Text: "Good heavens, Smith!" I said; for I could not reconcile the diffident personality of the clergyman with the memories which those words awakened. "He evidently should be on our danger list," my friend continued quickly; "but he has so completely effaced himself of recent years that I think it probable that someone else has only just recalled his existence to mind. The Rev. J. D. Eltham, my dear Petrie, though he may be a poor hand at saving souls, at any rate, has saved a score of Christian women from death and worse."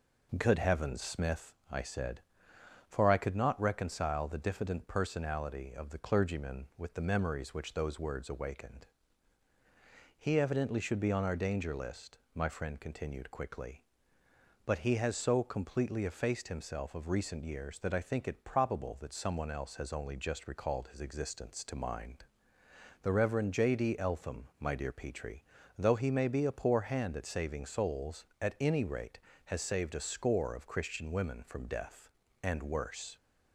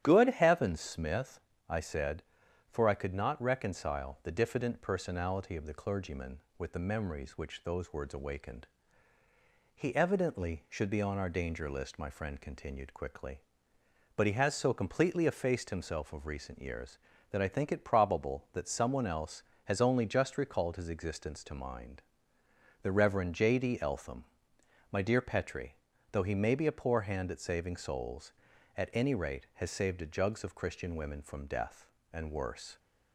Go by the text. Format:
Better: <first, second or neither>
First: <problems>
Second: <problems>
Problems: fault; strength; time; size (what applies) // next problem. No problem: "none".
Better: first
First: none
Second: starts louder than the rest; strong; until 1.0 s; 10.5 dB // says "jugs" for "score"; at 30.0 s